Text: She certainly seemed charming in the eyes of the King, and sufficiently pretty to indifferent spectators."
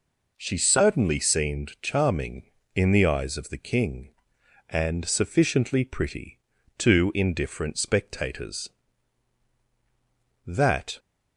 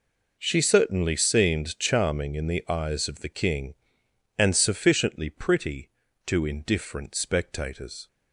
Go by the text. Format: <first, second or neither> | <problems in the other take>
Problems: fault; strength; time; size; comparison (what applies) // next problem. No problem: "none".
second | goes on to say "That"; from 10.4 s on; 0.54 s long